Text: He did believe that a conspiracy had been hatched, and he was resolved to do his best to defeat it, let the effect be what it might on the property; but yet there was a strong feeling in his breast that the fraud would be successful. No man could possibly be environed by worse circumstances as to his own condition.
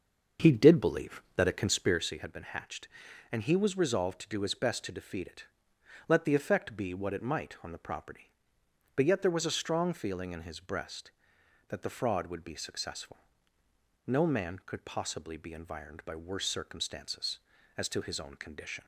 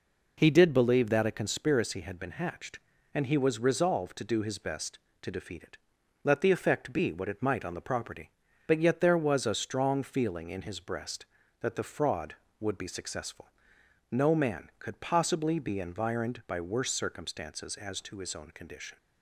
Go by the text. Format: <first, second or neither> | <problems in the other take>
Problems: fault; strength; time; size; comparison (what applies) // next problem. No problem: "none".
second | starts louder than the rest; until 2.1 s; 6.5 dB